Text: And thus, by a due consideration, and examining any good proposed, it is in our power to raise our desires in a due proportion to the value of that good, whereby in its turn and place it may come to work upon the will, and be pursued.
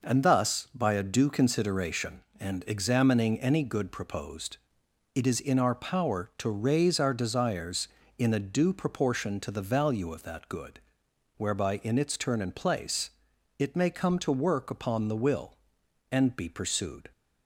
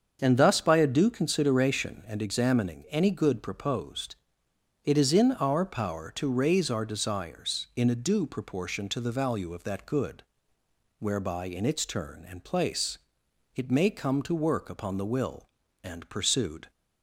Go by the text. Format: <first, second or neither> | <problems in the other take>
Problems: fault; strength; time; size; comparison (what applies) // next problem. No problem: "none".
first | starts louder than the rest; until 1.2 s; 7 dB // pauses between "place" and "it"; noticeable; at 12.9 s; 0.58 s long; noticeable in the first // skips "be"; at 16.0 s